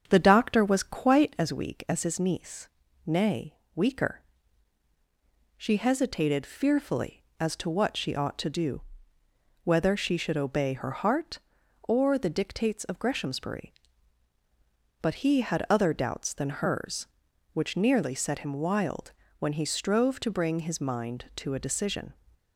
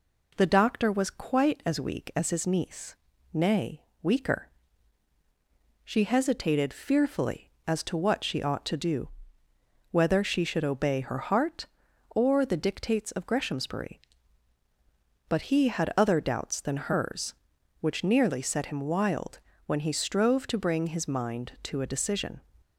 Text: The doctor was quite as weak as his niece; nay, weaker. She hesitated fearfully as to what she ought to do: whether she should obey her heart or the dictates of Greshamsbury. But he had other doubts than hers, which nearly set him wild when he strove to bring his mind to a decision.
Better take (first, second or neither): second